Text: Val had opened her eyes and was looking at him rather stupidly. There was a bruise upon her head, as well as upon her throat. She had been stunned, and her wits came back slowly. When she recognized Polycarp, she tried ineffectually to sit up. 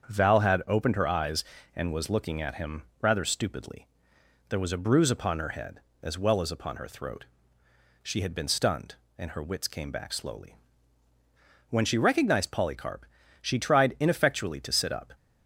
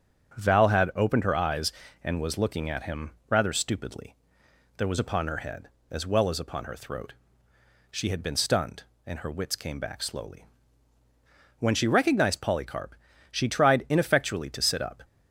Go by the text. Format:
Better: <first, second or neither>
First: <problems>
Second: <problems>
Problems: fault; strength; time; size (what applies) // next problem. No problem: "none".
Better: first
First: starts louder than the rest; strong; until 1.1 s; 7.5 dB // pauses between "him" and "rather"; slight; at 2.8 s; 0.18 s long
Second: starts louder than the rest; strong; until 1.4 s; 8 dB // pauses between "him" and "rather"; slight; at 3.1 s; 0.18 s long // skips "a bruise"; at 4.9 s